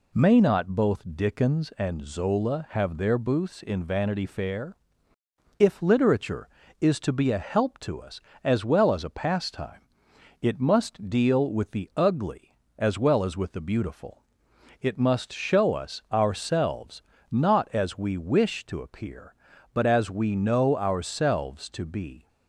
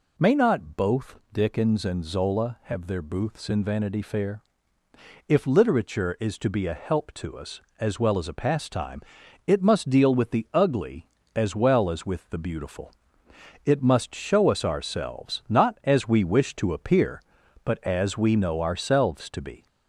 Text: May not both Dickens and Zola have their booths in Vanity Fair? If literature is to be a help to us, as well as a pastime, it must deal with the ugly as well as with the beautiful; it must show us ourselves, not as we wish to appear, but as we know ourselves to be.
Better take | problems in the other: first | gets louder; slight; throughout; 2 dB

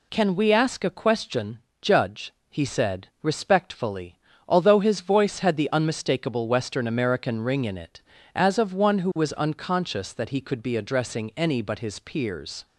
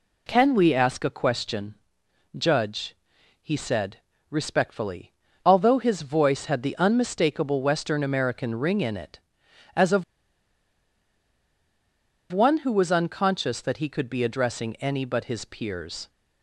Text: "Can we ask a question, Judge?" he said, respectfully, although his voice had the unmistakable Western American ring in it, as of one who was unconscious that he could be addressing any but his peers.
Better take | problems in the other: first | pauses between "of" and "one"; strong; at 10.0 s; 2.2 s long

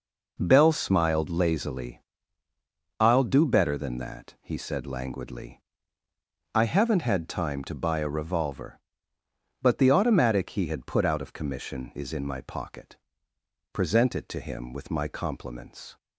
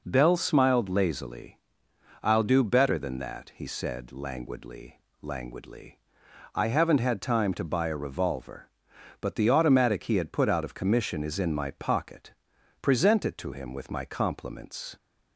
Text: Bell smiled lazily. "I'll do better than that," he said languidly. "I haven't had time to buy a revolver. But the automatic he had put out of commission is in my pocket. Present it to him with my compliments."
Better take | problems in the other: first | says "languidly" twice; at 5.2 s

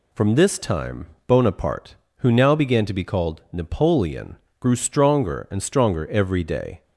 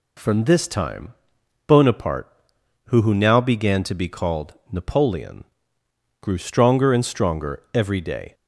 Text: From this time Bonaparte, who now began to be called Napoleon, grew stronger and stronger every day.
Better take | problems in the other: first | pauses between "time" and "Bonaparte"; noticeable; at 1.1 s; 0.54 s long; slight in the first // says "who" twice; at 3.0 s // pauses between "called" and "Napoleon"; slight; at 4.5 s; 0.18 s long

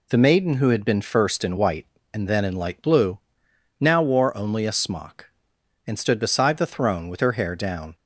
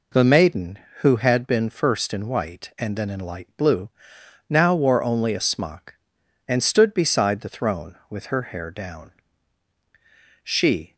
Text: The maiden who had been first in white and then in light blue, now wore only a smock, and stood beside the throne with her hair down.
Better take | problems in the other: first | goes on to say "She"; from 10.4 s on; 0.52 s long

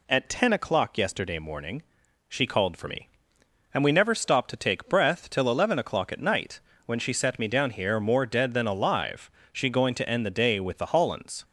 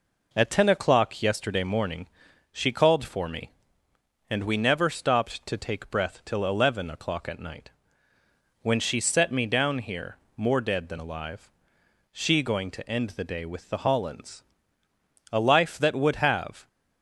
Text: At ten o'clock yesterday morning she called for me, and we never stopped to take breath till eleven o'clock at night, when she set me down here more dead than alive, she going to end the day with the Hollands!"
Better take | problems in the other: first | pauses between "morning" and "she"; noticeable; at 2.0 s; 0.46 s long; noticeable in the first // pauses between "here" and "more"; slight; at 10.1 s; 0.20 s long // goes on to say "A life that would have"; from 15.3 s on; 1.3 s long

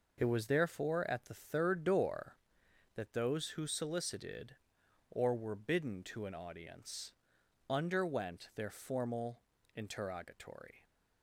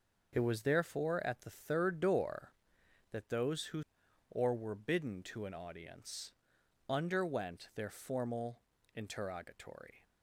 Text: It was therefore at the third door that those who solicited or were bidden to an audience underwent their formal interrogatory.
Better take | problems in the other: first | skips "solicited"; at 4.0 s // pauses between "audience" and "underwent"; noticeable; at 6.3 s; 0.58 s long; noticeable in the first // pauses between "formal" and "interrogatory"; slight; at 8.6 s; 0.34 s long; slight in the first

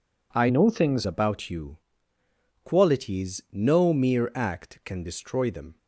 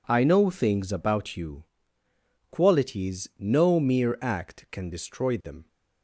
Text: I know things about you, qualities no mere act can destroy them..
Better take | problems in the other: second | changes voice from "know" to "things"; from 0.4 to 1.0 s; 0.6 s long

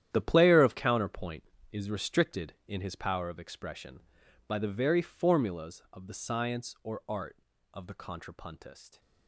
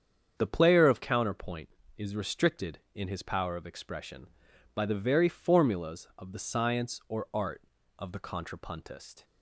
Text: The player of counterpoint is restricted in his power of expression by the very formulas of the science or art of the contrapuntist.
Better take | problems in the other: second | gets quieter; strong; throughout; 13 dB // starts louder than the rest; strong; until 1.1 s; 10.5 dB; strong in the second

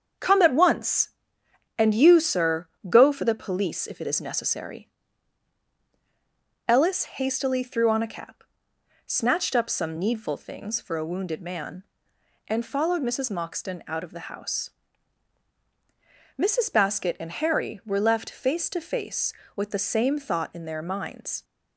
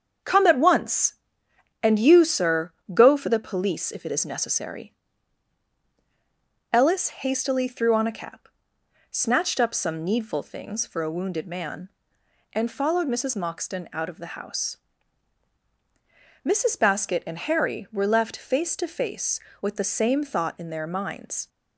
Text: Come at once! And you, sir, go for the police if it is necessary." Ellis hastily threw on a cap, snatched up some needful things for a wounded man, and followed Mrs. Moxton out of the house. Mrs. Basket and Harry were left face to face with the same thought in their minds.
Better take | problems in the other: neither | starts louder than the rest; strong; the same in both

